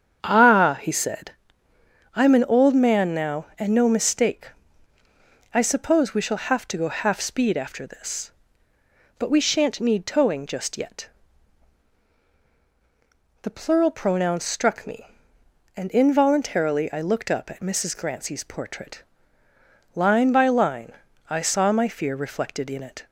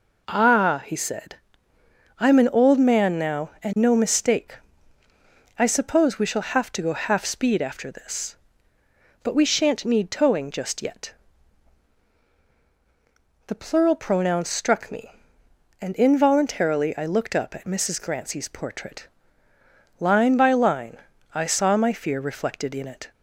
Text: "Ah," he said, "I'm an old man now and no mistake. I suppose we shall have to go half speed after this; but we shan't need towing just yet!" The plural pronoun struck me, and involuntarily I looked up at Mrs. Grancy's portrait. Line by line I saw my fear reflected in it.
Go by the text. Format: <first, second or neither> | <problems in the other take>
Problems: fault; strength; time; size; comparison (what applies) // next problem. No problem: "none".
second | starts louder than the rest; strong; until 1.4 s; 8 dB // pauses between "line" and "I"; slight; at 20.9 s; 0.36 s long; slight in the second